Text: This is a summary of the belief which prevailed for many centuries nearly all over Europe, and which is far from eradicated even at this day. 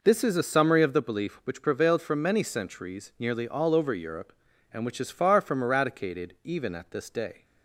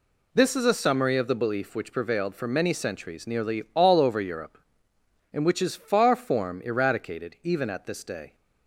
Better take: first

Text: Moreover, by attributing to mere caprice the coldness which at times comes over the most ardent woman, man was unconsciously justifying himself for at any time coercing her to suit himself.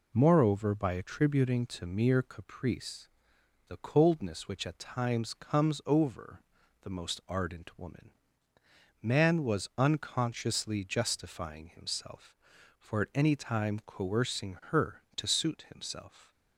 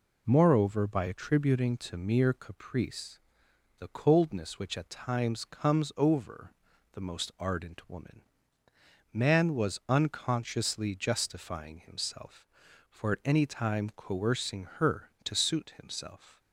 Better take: neither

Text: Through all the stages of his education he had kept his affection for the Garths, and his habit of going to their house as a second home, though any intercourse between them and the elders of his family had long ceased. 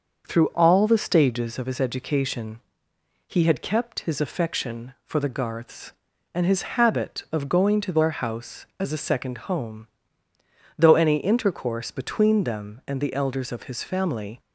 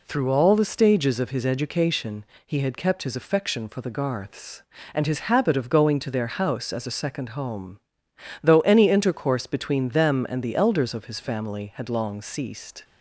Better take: second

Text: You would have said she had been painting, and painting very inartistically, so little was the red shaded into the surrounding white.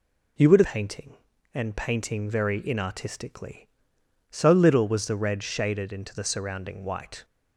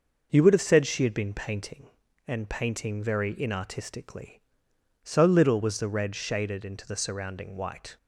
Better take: second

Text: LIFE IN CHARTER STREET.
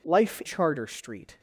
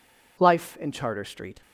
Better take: second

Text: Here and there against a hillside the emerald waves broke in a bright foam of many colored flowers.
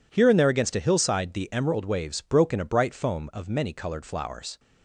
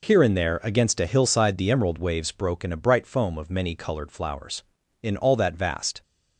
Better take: first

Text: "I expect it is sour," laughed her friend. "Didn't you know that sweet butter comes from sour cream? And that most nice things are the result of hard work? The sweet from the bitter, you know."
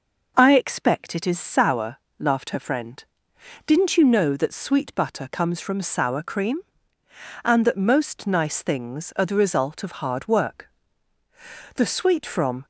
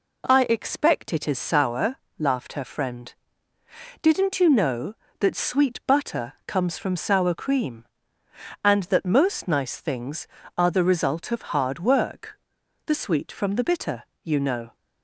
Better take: second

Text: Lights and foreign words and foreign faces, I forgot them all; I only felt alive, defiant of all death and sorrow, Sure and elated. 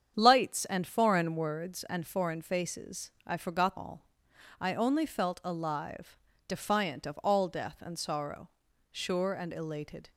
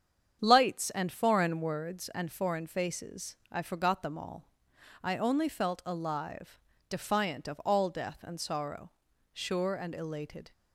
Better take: second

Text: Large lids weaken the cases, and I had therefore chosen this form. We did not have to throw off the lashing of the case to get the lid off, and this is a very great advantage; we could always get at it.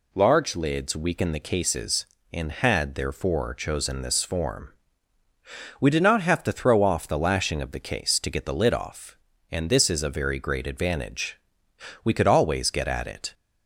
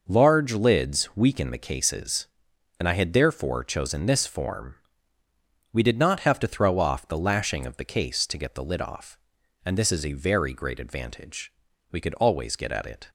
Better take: second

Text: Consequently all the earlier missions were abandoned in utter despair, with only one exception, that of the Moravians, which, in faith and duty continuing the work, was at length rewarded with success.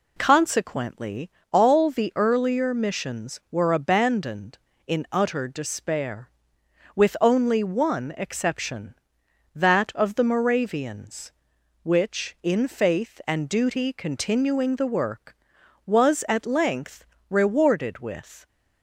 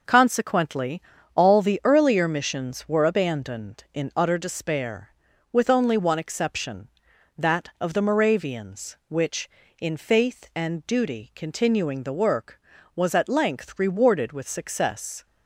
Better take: second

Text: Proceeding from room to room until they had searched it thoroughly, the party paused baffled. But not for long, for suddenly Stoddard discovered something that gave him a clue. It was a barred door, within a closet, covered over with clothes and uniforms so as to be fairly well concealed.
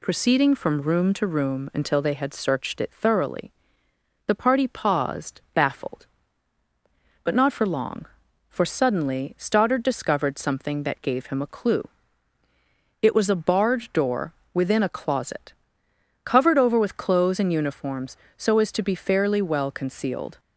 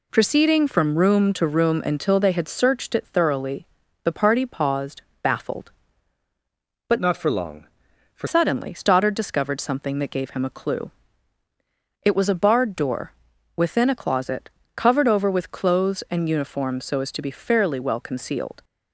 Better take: first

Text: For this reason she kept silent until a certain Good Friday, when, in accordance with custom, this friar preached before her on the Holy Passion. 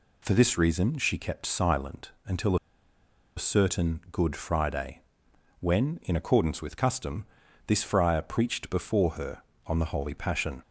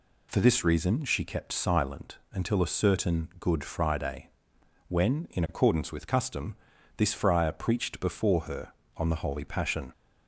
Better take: second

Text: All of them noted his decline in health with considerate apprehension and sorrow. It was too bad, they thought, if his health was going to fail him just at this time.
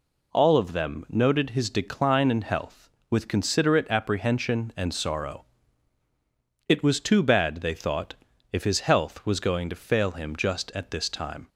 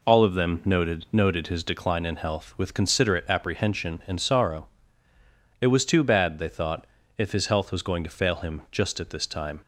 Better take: first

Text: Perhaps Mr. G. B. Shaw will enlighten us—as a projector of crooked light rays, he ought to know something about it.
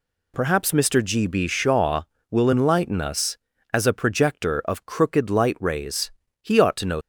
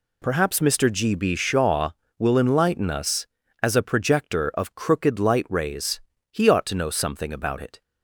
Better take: second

